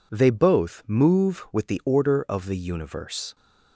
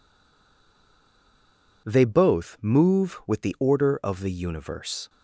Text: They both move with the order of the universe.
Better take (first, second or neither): first